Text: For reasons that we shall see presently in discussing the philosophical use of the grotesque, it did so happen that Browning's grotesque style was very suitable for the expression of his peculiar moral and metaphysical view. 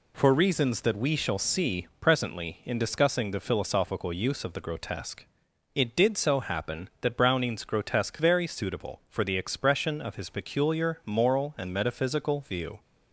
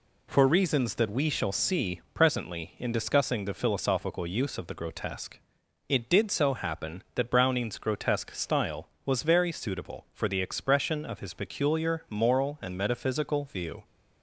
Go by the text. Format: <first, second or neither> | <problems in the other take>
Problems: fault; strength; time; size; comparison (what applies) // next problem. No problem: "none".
second | skips "style was"; at 8.1 s